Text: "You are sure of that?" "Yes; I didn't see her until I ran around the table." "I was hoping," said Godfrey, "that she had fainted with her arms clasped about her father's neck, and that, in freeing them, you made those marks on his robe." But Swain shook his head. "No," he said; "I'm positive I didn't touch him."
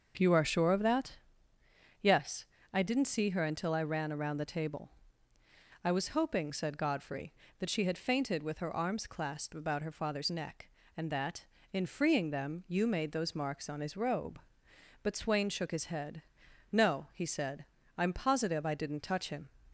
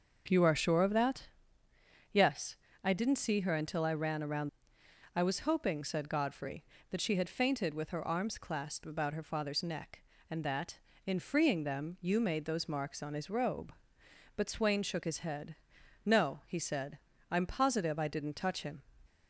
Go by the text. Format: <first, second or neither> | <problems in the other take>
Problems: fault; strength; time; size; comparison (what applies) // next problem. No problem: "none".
first | starts louder than the rest; noticeable; until 1.2 s; 6 dB; noticeable in the first // skips "the table"; at 4.8 s